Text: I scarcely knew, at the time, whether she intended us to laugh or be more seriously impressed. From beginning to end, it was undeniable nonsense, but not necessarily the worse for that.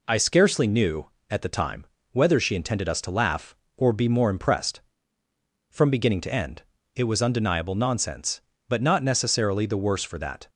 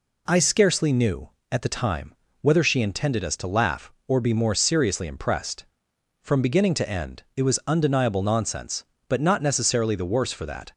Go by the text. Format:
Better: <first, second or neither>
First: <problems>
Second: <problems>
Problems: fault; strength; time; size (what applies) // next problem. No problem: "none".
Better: second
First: skips "seriously"; at 4.2 s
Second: none